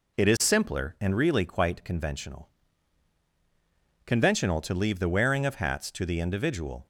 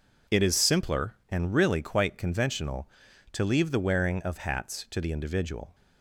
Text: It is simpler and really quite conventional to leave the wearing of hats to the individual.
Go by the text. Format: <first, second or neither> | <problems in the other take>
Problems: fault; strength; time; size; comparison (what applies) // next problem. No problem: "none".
second | says "conventional" twice; at 4.0 s